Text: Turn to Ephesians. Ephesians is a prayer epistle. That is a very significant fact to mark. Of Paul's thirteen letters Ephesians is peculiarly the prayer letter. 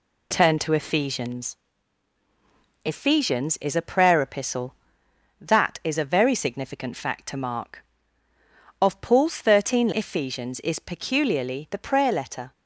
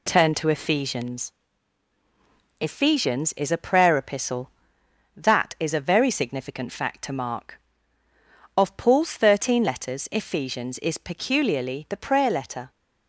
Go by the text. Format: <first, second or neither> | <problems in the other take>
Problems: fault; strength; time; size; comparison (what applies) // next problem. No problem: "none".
second | skips "letters"; at 9.9 s